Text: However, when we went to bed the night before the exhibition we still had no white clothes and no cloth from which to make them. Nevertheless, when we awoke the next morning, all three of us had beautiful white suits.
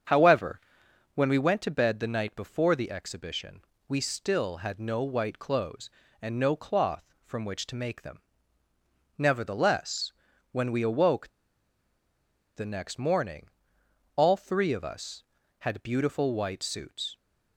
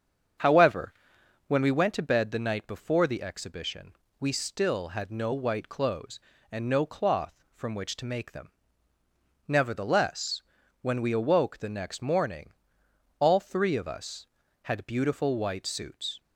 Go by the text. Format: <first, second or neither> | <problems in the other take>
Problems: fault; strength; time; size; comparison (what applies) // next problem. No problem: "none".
second | starts louder than the rest; strong; until 1.6 s; 7.5 dB; strong in the second // pauses between "exhibition" and "we"; slight; at 3.6 s; 0.26 s long; slight in the second // pauses between "awoke" and "the"; strong; at 11.2 s; 1.2 s long